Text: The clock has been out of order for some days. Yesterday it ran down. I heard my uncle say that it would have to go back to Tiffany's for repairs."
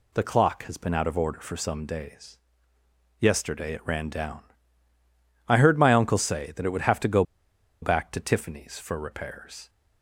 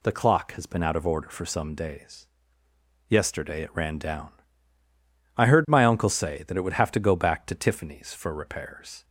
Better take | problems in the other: second | pauses between "go" and "back"; noticeable; at 7.2 s; 0.59 s long

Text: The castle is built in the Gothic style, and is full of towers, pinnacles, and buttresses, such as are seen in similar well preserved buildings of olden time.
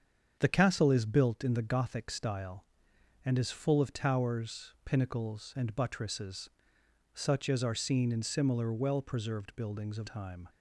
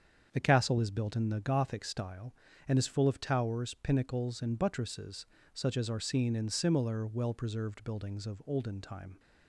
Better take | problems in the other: second | starts louder than the rest; strong; until 1.4 s; 7.5 dB; strong in the second // skips "olden"; at 10.0 s

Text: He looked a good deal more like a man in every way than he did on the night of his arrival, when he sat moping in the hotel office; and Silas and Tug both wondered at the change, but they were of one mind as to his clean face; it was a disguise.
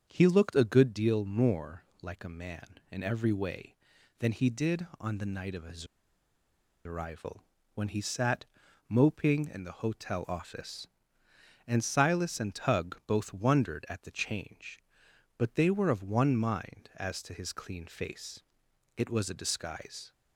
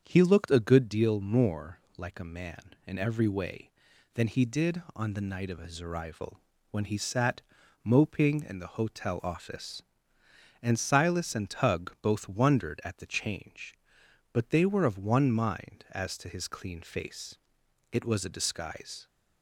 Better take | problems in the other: second | starts louder than the rest; until 1.0 s; 7 dB; strong in the second // pauses between "more" and "like"; slight; at 1.8 s; 0.18 s long; slight in the second // pauses between "his" and "arrival"; at 5.8 s; 1.0 s long // pauses between "sat" and "moping"; at 8.4 s; 0.44 s long; also in the second

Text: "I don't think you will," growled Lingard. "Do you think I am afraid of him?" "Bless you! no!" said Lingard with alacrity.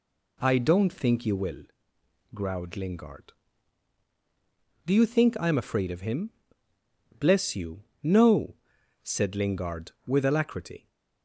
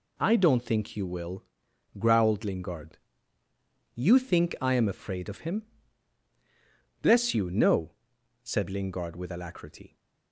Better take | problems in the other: first | skips "Do"; at 3.4 s

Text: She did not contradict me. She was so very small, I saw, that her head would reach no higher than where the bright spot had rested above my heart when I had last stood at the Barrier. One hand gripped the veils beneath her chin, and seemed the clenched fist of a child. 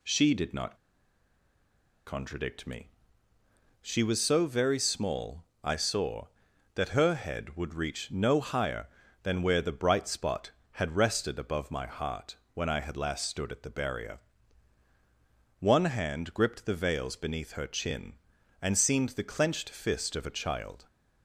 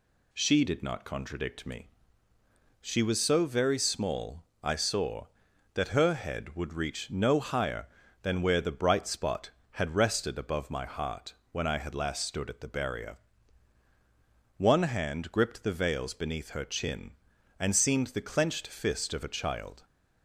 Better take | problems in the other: second | pauses between "not" and "contradict"; strong; at 0.7 s; 1.3 s long // pauses between "heart" and "when"; slight; at 12.3 s; 0.18 s long; slight in the second

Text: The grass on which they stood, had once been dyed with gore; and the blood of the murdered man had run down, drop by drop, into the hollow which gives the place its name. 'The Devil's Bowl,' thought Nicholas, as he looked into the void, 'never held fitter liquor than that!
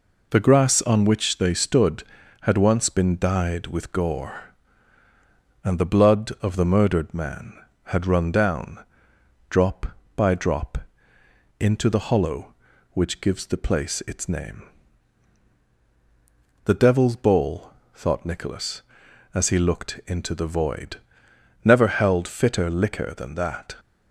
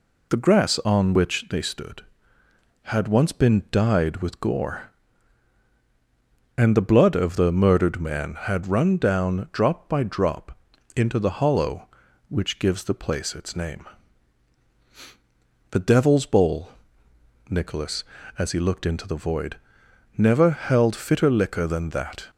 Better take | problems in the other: first | skips "thought"; at 17.0 s

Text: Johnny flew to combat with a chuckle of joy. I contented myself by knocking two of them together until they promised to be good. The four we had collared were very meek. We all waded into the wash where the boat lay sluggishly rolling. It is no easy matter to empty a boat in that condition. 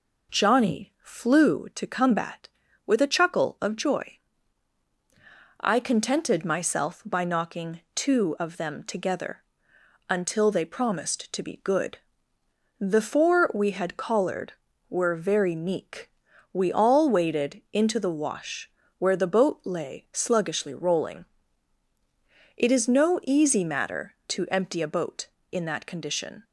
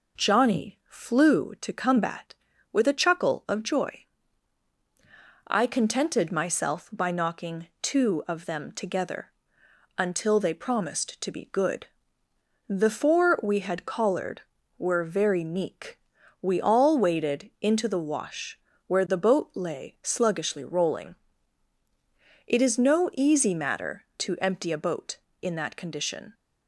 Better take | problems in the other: neither | pauses between "knocking" and "two"; slight; the same in both // pauses between "together" and "until"; noticeable; the same in both // pauses between "wash" and "where"; slight; the same in both

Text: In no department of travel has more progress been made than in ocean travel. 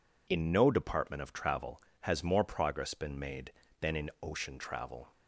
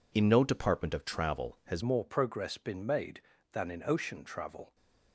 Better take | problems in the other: first | changes voice at "more"; from 1.8 s on; 2.9 s long

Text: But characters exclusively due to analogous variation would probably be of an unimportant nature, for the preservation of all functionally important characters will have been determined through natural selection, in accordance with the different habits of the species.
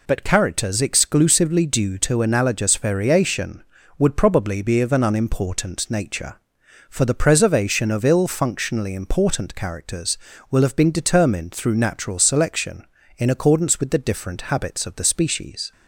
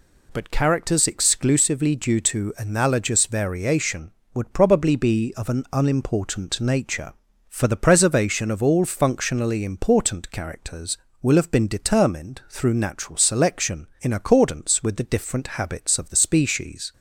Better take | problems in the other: second | says "ill" for "all"; at 8.0 s

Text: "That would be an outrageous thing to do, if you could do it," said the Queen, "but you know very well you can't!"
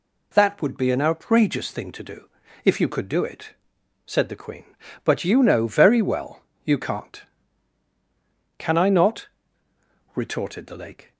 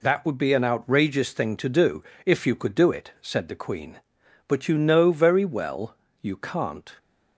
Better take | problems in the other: second | pauses between "well" and "you"; slight; at 6.4 s; 0.22 s long; slight in the second // goes on to say "Can I not retorted the Lake"; strong; from 8.5 s on; 2.5 s long

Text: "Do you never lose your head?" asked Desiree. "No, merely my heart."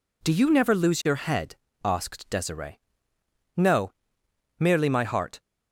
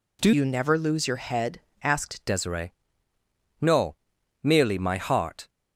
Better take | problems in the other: first | changes voice from "you" to "asked"; from 0.3 to 2.2 s; 1.9 s long

